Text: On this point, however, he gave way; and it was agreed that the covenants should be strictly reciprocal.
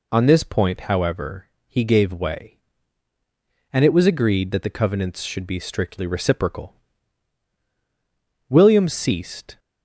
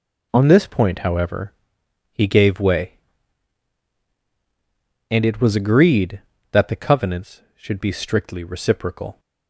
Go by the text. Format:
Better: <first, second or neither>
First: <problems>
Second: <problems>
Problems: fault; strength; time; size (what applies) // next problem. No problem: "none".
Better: second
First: goes on to say "William ceased"; noticeable; from 8.4 s on; 1.1 s long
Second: none